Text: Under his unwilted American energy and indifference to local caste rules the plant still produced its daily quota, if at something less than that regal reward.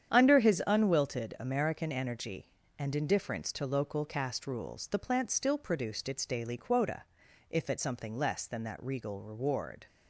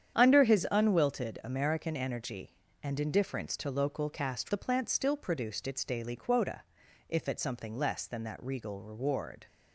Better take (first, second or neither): first